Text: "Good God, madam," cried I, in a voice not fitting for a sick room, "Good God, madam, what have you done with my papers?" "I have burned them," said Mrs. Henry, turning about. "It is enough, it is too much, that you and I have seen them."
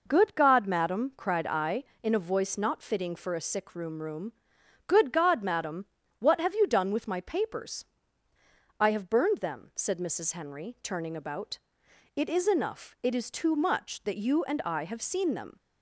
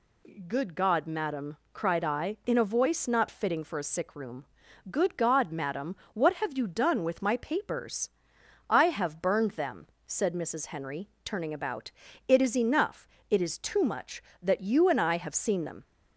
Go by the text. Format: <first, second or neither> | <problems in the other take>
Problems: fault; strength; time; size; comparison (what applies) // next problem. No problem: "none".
second | says "room" twice; at 4.0 s